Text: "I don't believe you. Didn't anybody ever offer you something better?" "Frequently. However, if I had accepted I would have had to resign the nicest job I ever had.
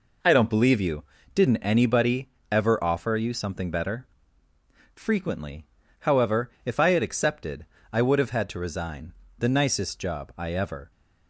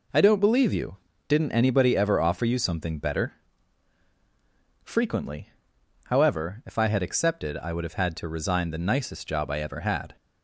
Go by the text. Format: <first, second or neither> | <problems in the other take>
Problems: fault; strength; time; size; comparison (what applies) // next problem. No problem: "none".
second | pauses between "anybody" and "ever"; slight; at 2.2 s; 0.22 s long // pauses between "accepted" and "I"; slight; at 7.6 s; 0.26 s long // pauses between "resign" and "the"; slight; at 9.1 s; 0.24 s long // stops before "had"; at 10.9 s